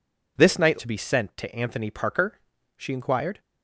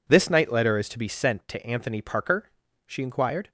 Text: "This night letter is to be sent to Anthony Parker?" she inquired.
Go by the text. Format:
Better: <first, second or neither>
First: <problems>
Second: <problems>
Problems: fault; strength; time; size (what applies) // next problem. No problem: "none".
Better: second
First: skips "letter is"; at 0.7 s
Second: none